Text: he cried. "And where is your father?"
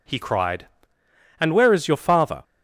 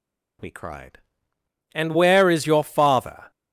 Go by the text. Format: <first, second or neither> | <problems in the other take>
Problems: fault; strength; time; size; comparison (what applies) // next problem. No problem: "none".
first | says "we" for "he"; at 0.4 s